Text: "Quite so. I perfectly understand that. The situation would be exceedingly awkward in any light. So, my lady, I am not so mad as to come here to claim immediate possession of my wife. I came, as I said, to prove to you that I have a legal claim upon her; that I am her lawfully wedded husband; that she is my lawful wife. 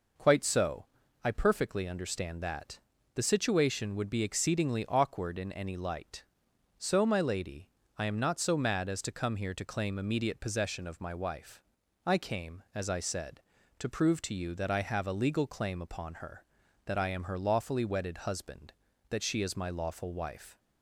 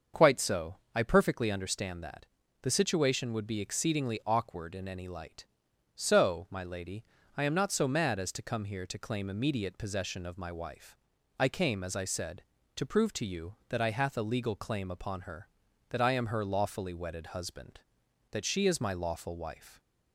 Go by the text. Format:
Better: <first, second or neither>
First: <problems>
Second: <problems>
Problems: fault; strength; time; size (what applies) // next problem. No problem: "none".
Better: first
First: none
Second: starts louder than the rest; until 1.3 s; 6.5 dB // says "hath" for "have"; at 13.9 s